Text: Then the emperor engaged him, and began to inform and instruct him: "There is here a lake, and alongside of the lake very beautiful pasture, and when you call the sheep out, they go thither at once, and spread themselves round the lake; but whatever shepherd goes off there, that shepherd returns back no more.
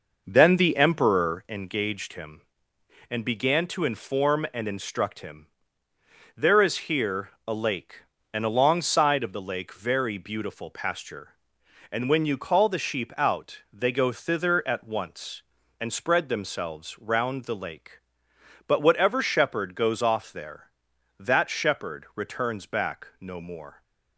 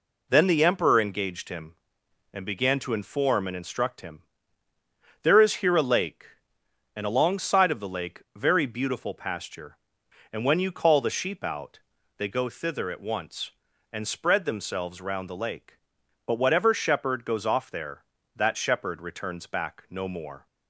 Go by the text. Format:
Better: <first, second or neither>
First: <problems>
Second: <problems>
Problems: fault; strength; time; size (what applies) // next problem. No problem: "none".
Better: second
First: starts louder than the rest; noticeable; until 1.6 s; 5.5 dB // pauses between "here" and "a"; slight; at 7.2 s; 0.18 s long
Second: none